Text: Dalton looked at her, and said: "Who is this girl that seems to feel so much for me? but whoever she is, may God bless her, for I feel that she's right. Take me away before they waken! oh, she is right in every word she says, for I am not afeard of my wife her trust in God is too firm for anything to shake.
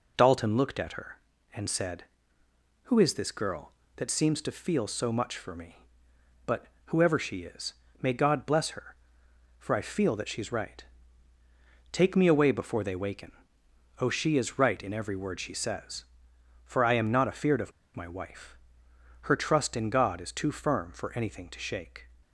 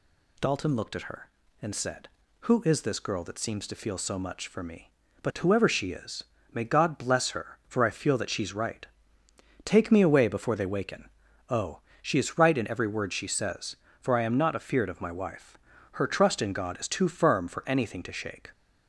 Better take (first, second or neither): second